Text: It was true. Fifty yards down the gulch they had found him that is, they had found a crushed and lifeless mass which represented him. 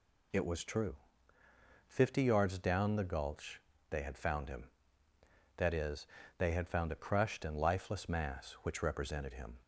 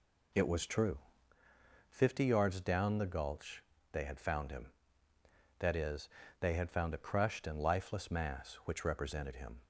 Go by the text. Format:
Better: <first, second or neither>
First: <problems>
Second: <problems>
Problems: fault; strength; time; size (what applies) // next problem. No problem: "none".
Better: first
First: pauses between "gulch" and "they"; slight; at 3.6 s; 0.30 s long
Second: starts louder than the rest; slight; until 1.3 s; 2.5 dB // pauses between "gulch" and "they"; slight; at 3.6 s; 0.30 s long